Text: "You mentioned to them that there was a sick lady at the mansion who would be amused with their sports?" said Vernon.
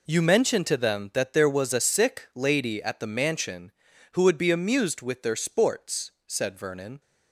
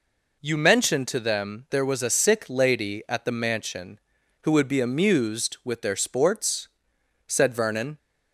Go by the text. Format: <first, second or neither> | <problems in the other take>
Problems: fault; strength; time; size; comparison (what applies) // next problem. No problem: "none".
first | skips "that"; at 1.6 s